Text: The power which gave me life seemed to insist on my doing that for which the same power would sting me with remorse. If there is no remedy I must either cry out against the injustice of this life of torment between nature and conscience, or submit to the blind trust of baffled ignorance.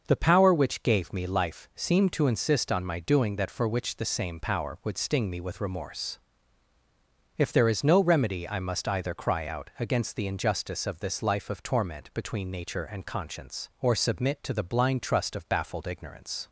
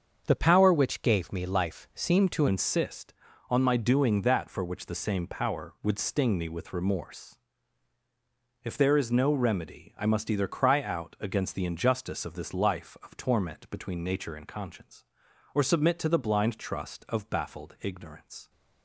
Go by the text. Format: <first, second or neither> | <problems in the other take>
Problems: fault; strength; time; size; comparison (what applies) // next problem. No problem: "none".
first | starts louder than the rest; strong; until 1.2 s; 7 dB // changes voice at "insist"; from 2.4 s on; 16.0 s long